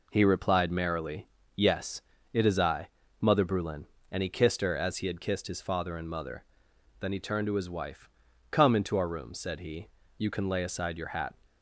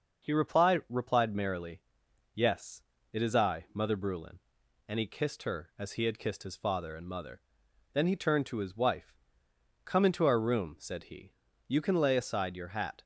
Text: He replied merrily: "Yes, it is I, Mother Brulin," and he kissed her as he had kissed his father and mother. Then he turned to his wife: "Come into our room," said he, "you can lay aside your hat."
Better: first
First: none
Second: starts louder than the rest; noticeable; until 1.2 s; 6 dB // says "replied" twice; at 0.8 s

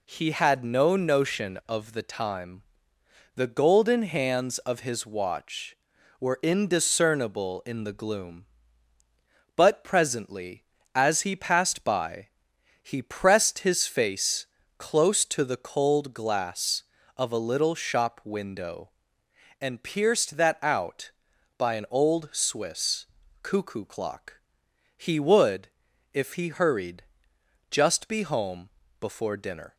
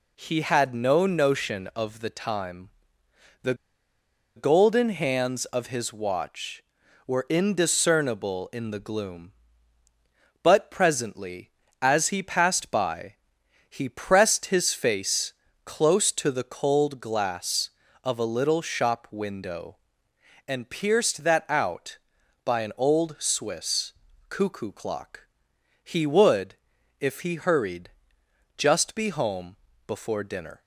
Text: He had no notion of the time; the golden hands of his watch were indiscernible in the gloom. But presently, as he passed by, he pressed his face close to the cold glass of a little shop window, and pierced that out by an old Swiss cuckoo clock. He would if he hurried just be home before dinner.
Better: first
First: pauses between "face" and "close"; slight; at 14.4 s; 0.32 s long // pauses between "Swiss" and "cuckoo"; at 23.0 s; 0.38 s long // pauses between "would" and "if"; noticeable; at 25.6 s; 0.46 s long // pauses between "hurried" and "just"; noticeable; at 27.0 s; 0.66 s long // pauses between "home" and "before"; slight; at 28.7 s; 0.30 s long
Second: pauses between "the" and "golden"; noticeable; at 3.5 s; 0.82 s long // pauses between "face" and "close"; slight; at 15.3 s; 0.32 s long // pauses between "Swiss" and "cuckoo"; at 23.9 s; 0.38 s long // pauses between "would" and "if"; noticeable; at 26.5 s; 0.46 s long // pauses between "hurried" and "just"; noticeable; at 27.8 s; 0.66 s long // pauses between "home" and "before"; slight; at 29.5 s; 0.30 s long

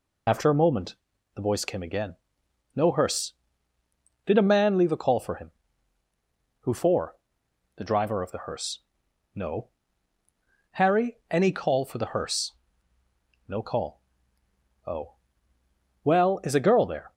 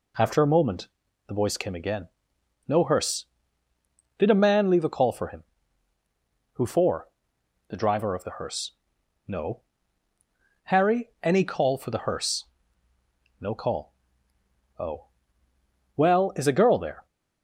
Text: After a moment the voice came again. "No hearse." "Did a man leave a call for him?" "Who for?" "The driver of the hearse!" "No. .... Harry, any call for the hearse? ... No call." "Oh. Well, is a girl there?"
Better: second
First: loses the start of "After"; at 0.2 s; 40 ms // pauses between "moment" and "the"; at 0.9 s; 0.40 s long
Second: pauses between "moment" and "the"; at 0.8 s; 0.40 s long

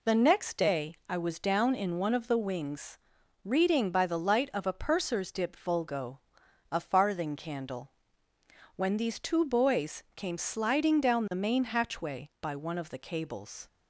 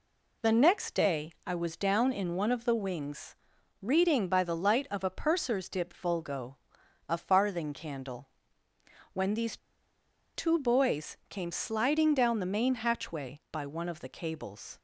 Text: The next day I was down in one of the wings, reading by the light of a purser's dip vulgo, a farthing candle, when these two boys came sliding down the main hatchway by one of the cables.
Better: first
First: none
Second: pauses between "these" and "two"; noticeable; at 9.5 s; 0.78 s long

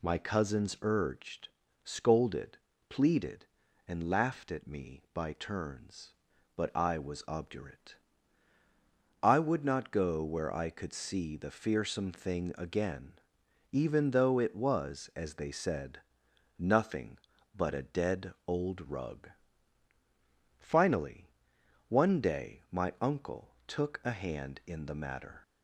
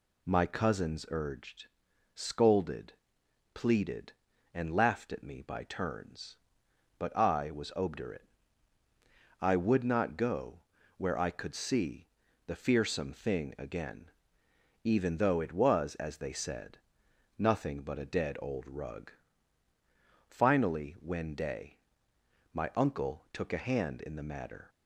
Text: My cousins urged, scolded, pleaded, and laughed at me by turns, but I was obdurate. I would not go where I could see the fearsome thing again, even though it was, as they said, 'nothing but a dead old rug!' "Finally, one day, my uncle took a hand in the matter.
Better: first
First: none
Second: pauses between "go" and "where"; at 10.5 s; 0.38 s long // pauses between "see" and "the"; at 12.0 s; 0.40 s long // says "when" for "one"; at 20.9 s

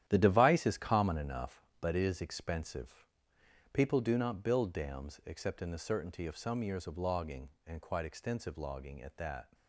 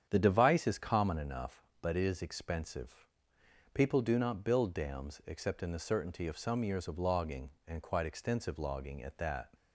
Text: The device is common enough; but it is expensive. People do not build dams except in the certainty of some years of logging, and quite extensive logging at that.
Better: second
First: gets quieter; strong; throughout; 10 dB // starts louder than the rest; strong; until 1.0 s; 11 dB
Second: starts louder than the rest; strong; until 1.1 s; 8.5 dB

